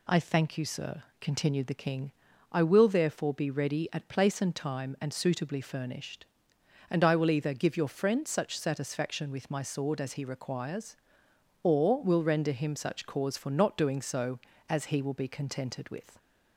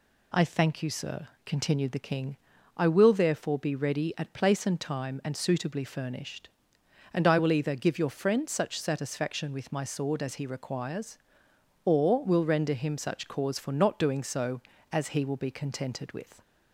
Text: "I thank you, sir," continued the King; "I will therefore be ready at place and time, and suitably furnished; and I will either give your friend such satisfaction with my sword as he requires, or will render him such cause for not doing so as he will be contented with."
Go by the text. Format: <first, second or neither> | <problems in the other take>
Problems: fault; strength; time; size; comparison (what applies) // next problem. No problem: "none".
neither | none